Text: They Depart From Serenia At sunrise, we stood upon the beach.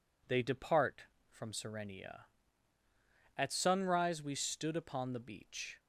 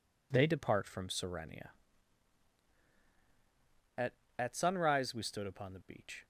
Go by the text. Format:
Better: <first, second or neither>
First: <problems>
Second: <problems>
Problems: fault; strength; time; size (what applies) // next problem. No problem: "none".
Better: first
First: none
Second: says "At" twice; at 4.3 s